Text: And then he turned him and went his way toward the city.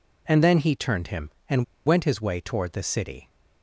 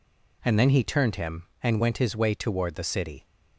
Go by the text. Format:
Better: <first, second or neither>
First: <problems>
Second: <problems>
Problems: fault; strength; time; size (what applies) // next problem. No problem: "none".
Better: second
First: pauses between "and" and "went"; slight; at 1.6 s; 0.22 s long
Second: none